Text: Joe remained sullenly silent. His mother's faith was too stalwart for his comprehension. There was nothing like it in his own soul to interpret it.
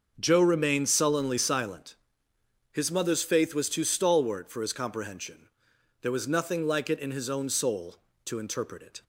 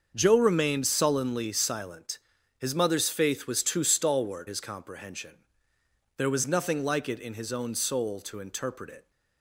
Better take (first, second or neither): first